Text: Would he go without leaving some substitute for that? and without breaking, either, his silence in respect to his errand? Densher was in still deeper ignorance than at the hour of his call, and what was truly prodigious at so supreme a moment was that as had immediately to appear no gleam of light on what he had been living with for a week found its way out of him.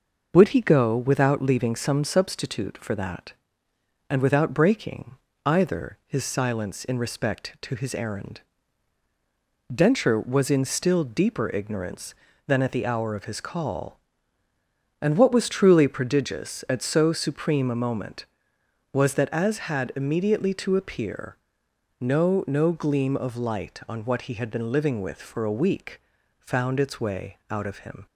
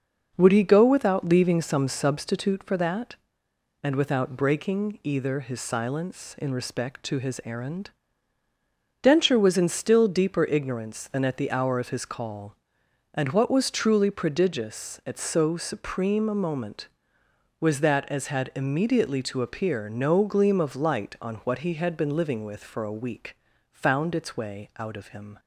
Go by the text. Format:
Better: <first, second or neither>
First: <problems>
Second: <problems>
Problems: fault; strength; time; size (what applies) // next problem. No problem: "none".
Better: second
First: pauses between "appear" and "no"; noticeable; at 21.3 s; 0.60 s long // says "no" twice; at 22.4 s // pauses between "week" and "found"; slight; at 26.0 s; 0.36 s long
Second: pauses between "week" and "found"; slight; at 23.3 s; 0.34 s long